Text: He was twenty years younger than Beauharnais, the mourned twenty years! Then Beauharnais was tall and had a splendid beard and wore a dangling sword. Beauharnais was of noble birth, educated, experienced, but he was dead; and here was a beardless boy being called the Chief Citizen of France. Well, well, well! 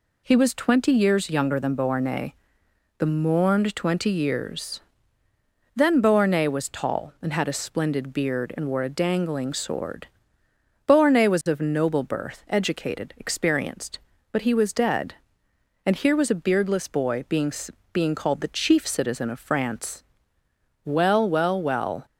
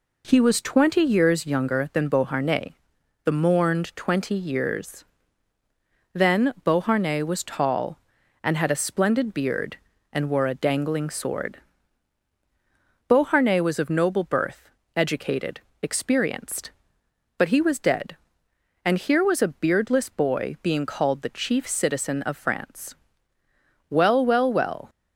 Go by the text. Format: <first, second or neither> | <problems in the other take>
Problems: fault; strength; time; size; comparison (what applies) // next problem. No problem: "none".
second | says "being" twice; at 17.9 s